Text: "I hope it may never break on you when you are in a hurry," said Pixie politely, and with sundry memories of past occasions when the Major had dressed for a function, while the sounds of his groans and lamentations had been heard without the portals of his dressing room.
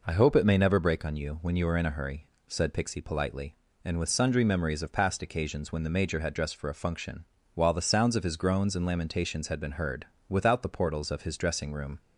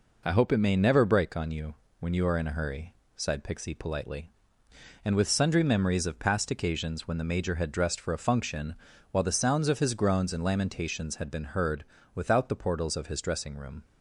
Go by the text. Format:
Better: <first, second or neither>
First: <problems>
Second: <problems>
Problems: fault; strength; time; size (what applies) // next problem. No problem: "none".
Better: first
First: pauses between "heard" and "without"; slight; at 10.0 s; 0.22 s long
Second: pauses between "you" and "when"; slight; at 1.7 s; 0.26 s long // says "sighed" for "said"; at 3.1 s // pauses between "heard" and "without"; slight; at 11.8 s; 0.30 s long